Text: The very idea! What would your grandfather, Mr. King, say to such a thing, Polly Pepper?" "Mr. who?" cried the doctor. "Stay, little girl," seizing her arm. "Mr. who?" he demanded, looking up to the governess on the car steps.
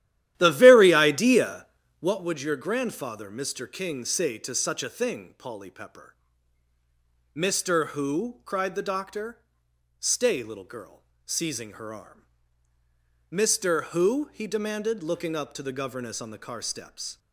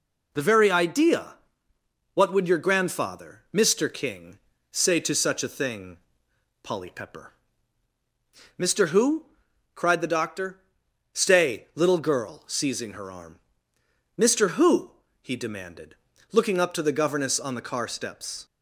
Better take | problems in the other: second | starts louder than the rest; strong; until 2.2 s; 12.5 dB

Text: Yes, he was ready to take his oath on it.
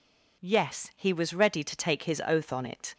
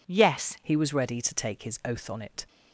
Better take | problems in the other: first | changes voice at "he"; from 0.6 s on; 1.8 s long

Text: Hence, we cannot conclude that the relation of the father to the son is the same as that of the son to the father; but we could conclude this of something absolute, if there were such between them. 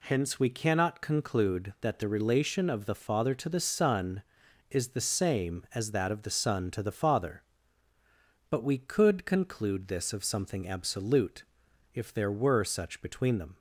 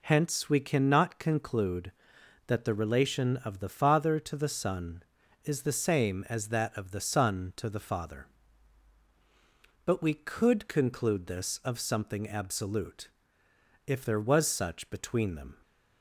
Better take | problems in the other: first | says "was" for "were"; at 14.1 s

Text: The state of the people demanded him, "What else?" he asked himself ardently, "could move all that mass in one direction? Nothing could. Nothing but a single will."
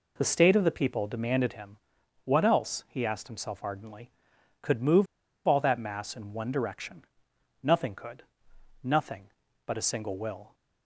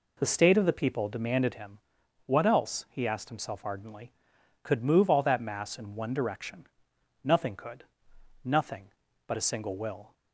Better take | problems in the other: second | pauses between "move" and "all"; at 5.0 s; 0.39 s long

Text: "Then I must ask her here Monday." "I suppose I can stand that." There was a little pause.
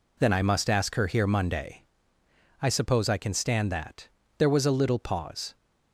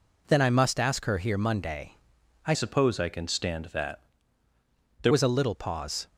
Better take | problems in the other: first | changes voice from "suppose" to "There"; from 2.5 to 5.1 s; 2.6 s long

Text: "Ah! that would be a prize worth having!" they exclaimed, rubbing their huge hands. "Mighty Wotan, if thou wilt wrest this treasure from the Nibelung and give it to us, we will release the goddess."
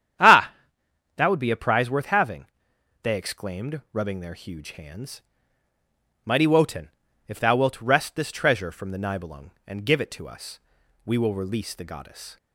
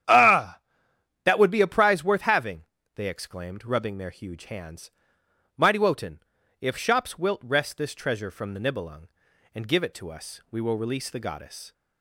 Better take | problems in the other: first | starts louder than the rest; strong; until 1.7 s; 10 dB; strong in the first // says "shops" for "thou"; at 6.7 s

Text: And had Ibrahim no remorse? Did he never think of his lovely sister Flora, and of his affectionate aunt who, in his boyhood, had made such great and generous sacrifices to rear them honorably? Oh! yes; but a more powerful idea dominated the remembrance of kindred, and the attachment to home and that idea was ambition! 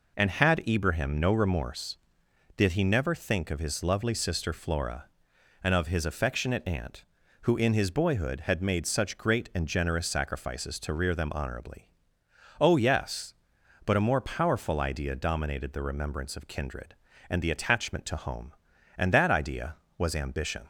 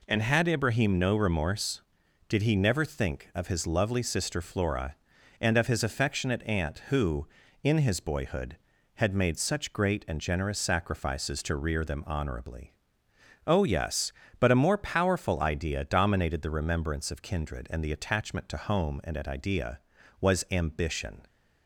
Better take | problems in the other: first | says "at" for "that"; at 19.1 s

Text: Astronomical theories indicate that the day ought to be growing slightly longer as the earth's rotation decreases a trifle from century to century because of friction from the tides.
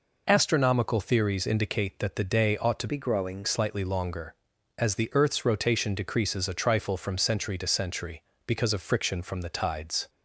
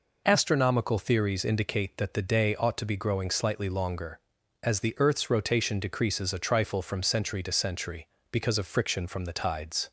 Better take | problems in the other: second | changes voice from "be" to "growing"; from 2.8 to 3.4 s; 0.6 s long

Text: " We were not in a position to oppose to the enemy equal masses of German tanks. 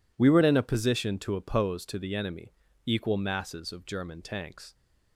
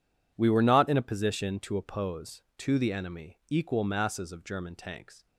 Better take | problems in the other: second | skips "not"; at 0.4 s // pauses between "enemy" and "equal"; slight; at 2.5 s; 0.32 s long

